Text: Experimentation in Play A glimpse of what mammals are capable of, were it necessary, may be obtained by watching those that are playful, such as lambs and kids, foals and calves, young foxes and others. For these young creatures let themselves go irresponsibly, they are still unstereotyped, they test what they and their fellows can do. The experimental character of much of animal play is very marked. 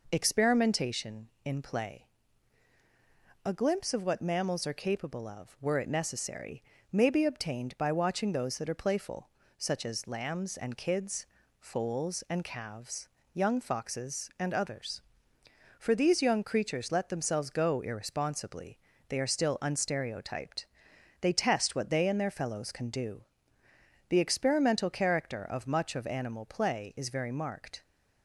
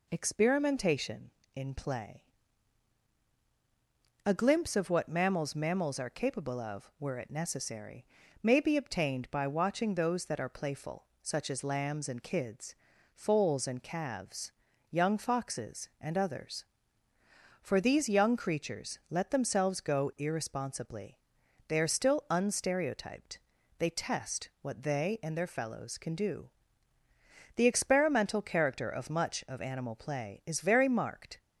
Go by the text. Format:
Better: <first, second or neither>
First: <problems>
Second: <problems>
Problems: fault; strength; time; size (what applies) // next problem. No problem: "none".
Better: first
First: pauses between "Play" and "A"; strong; at 2.0 s; 1.3 s long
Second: pauses between "Play" and "A"; strong; at 2.2 s; 2.0 s long // says "mammals" twice; at 5.5 s